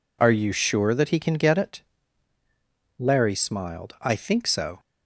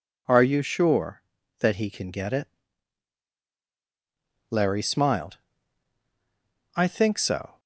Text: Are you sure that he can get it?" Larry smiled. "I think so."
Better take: neither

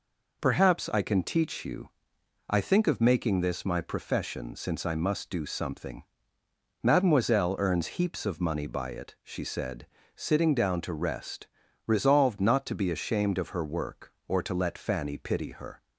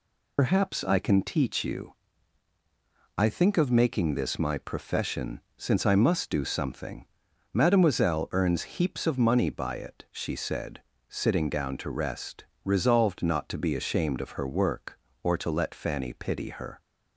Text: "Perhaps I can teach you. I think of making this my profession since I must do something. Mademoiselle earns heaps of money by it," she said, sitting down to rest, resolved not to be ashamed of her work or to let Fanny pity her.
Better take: first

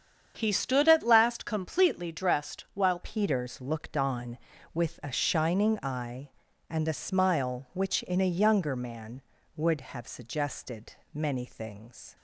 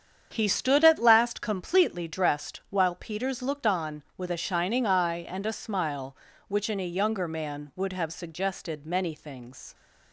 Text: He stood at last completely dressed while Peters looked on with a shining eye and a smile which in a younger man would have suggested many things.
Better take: second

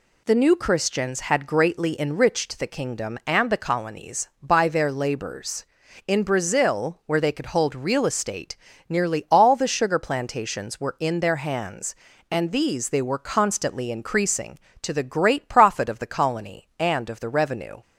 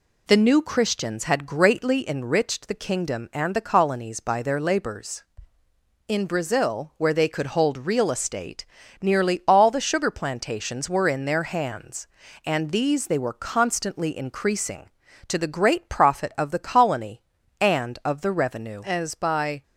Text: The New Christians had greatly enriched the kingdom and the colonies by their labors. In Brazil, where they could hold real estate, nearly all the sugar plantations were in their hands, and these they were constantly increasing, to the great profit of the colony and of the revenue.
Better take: first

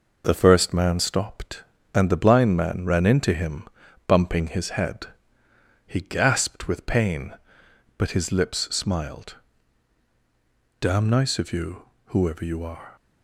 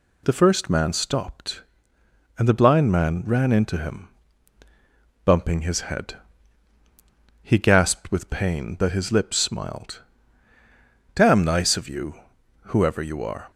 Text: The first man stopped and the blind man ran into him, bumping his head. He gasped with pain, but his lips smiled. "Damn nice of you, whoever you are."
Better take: second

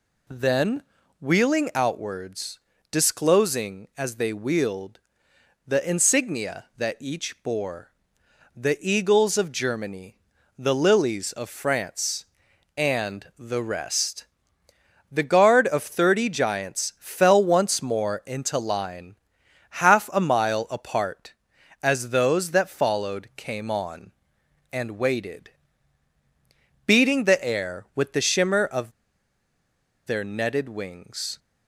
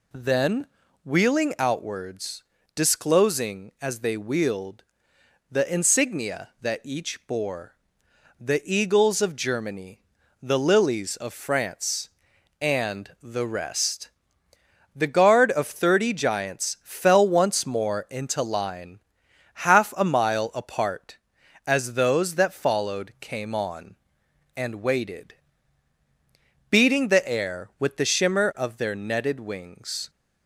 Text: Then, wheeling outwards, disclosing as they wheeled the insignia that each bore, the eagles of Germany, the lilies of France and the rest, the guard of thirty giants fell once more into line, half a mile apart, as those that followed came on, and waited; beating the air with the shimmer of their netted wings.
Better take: second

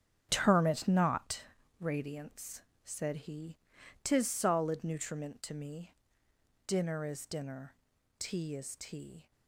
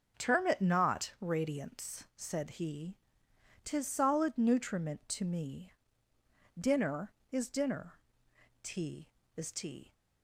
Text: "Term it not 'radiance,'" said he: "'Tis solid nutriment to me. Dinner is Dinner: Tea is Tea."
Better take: second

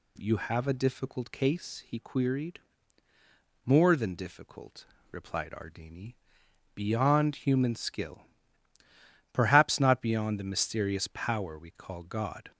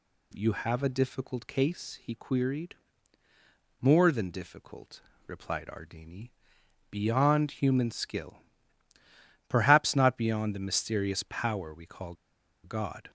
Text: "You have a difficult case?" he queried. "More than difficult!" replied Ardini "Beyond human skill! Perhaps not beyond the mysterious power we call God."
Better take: first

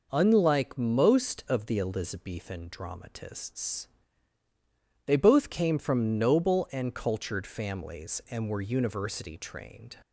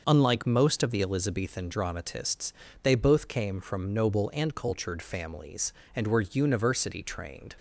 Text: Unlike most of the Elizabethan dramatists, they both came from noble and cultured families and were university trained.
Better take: neither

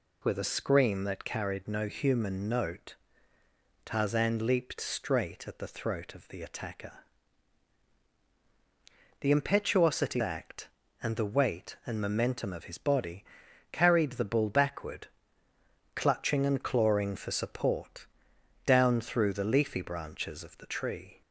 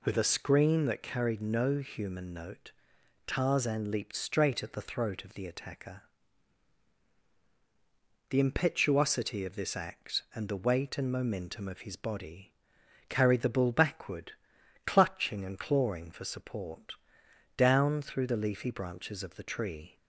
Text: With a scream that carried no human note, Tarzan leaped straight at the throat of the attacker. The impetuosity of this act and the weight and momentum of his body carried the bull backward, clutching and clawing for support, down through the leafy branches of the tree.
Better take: second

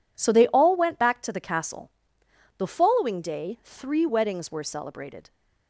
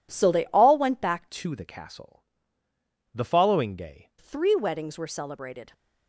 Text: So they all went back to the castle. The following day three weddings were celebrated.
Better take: first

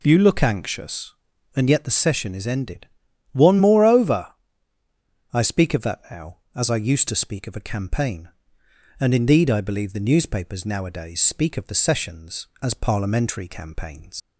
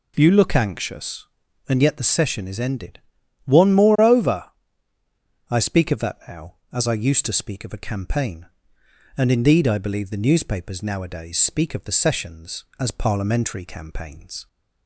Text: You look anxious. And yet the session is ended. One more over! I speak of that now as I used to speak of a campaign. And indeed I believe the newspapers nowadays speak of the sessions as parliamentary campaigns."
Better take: second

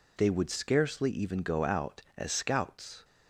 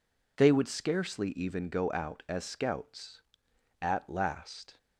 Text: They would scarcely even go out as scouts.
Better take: first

